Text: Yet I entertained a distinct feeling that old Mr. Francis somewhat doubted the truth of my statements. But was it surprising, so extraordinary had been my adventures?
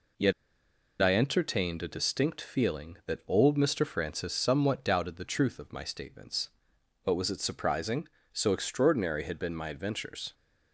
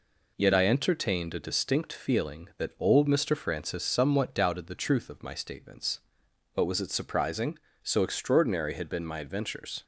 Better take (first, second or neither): second